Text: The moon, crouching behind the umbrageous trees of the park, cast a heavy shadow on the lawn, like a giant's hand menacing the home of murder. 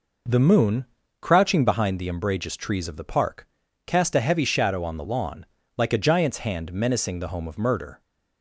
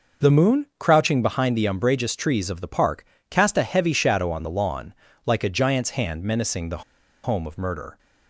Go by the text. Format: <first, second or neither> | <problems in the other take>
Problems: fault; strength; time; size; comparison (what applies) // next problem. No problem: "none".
first | pauses between "the" and "home"; at 6.8 s; 0.42 s long